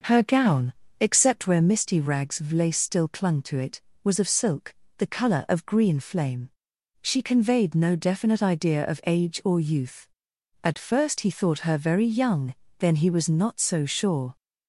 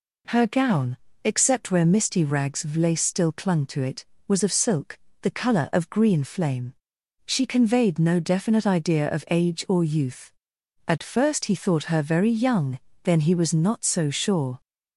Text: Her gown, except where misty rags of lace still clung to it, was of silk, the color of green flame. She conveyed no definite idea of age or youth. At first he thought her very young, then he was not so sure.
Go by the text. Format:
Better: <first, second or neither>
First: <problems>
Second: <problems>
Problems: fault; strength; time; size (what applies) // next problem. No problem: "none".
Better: second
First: starts louder than the rest; noticeable; until 1.7 s; 6 dB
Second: none